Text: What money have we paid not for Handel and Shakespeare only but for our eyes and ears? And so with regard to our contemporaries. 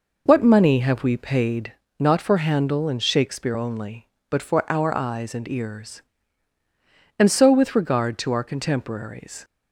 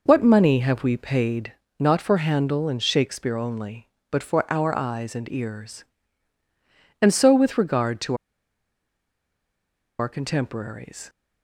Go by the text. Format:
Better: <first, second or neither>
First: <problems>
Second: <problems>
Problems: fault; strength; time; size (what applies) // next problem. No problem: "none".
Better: first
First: pauses between "paid" and "not"; slight; at 1.7 s; 0.30 s long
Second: pauses between "paid" and "not"; slight; at 1.5 s; 0.30 s long // pauses between "to" and "our"; strong; at 8.1 s; 1.8 s long